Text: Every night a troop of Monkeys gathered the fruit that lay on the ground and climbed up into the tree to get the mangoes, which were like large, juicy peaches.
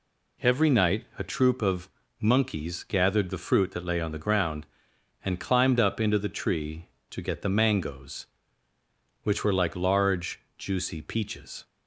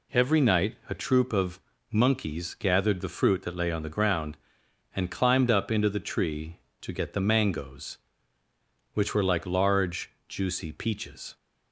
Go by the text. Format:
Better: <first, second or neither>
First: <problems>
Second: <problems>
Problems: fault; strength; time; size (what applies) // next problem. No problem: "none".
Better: neither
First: pauses between "of" and "Monkeys"; slight; at 1.8 s; 0.32 s long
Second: pauses between "of" and "Monkeys"; slight; at 1.5 s; 0.32 s long